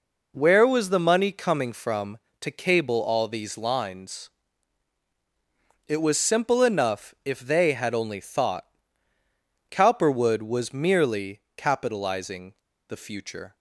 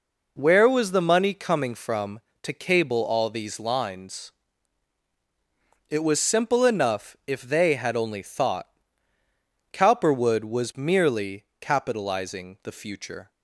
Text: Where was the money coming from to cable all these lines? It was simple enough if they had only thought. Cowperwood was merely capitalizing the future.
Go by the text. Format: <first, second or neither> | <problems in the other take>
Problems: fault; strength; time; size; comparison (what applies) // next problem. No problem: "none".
second | pauses between "merely" and "capitalizing"; slight; at 11.3 s; 0.16 s long; slight in the second // pauses between "capitalizing" and "the"; at 12.5 s; 0.36 s long